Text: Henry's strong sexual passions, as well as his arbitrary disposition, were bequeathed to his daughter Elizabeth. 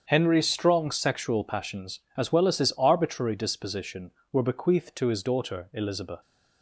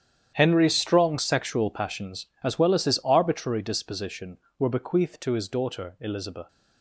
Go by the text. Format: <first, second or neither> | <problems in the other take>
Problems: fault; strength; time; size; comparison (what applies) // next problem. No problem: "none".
first | gets quieter; strong; throughout; 14.5 dB // starts louder than the rest; strong; until 1.3 s; 10 dB; strong in the first